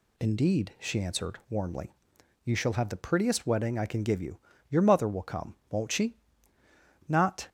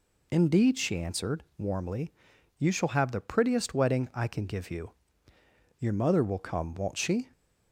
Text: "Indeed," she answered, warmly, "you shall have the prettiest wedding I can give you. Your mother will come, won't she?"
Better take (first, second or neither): second